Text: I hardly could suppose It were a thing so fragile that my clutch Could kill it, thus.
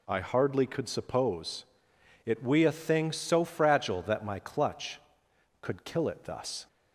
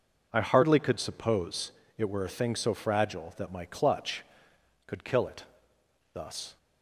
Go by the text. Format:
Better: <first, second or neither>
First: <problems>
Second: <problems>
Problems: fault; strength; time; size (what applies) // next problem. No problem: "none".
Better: second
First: pauses between "suppose" and "It"; noticeable; at 1.6 s; 0.60 s long // says "we" for "were"; at 2.4 s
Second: pauses between "suppose" and "It"; slight; at 1.7 s; 0.24 s long